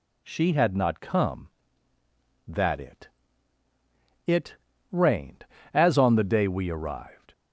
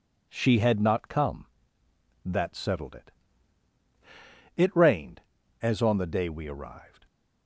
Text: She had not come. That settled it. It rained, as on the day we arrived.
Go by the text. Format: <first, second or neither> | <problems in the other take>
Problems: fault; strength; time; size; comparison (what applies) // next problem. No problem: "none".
second | skips "settled"; at 2.7 s // pauses between "It" and "rained"; slight; at 4.5 s; 0.34 s long